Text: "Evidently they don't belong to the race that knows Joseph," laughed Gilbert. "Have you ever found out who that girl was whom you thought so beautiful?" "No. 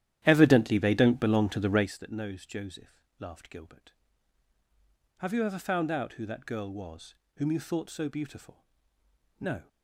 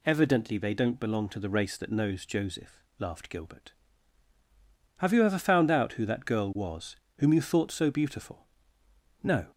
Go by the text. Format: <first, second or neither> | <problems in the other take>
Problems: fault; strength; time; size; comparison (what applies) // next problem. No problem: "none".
second | starts louder than the rest; strong; until 2.0 s; 12 dB // pauses between "was" and "whom"; slight; at 7.1 s; 0.22 s long; slight in the second